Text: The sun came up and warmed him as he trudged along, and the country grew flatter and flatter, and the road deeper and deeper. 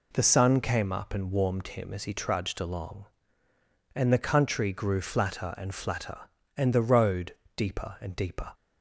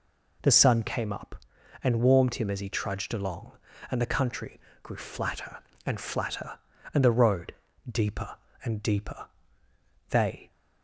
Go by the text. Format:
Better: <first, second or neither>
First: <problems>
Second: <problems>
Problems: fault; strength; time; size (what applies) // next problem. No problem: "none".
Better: first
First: pauses between "road" and "deeper"; slight; at 7.3 s; 0.22 s long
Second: pauses between "country" and "grew"; slight; at 4.5 s; 0.24 s long // pauses between "road" and "deeper"; at 7.5 s; 0.38 s long // goes on to say "They"; slight; from 10.0 s on; 0.42 s long